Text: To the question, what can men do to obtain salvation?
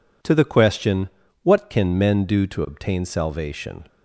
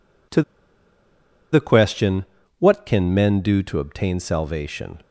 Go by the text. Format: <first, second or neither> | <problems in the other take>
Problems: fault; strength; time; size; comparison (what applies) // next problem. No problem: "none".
first | pauses between "To" and "the"; at 0.4 s; 1.1 s long